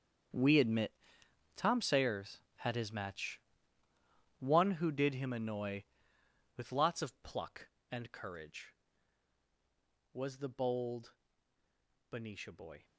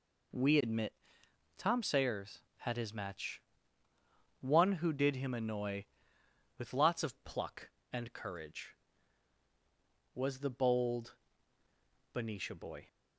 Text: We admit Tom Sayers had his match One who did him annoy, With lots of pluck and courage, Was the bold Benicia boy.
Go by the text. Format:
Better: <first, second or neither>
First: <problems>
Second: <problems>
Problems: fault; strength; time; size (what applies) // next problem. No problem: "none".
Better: second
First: gets quieter; strong; throughout; 14 dB // pauses between "admit" and "Tom"; noticeable; at 0.9 s; 0.64 s long // pauses between "match" and "One"; at 3.3 s; 1.0 s long // pauses between "bold" and "Benicia"; at 11.1 s; 0.98 s long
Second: pauses between "admit" and "Tom"; noticeable; at 0.9 s; 0.64 s long // pauses between "match" and "One"; at 3.3 s; 1.0 s long // pauses between "bold" and "Benicia"; at 11.1 s; 1.0 s long